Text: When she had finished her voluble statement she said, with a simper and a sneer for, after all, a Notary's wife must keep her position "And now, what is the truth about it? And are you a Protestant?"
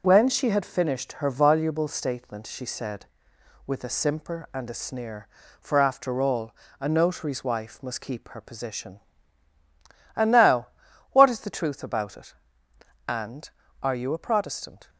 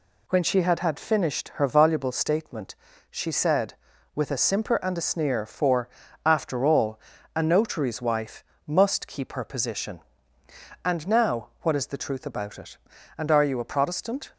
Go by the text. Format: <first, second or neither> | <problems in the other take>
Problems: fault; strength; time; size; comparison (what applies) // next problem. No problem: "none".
first | says "had" twice; at 0.7 s // pauses between "statement" and "she"; slight; at 2.7 s; 0.36 s long // pauses between "wife" and "must"; slight; at 8.4 s; 0.24 s long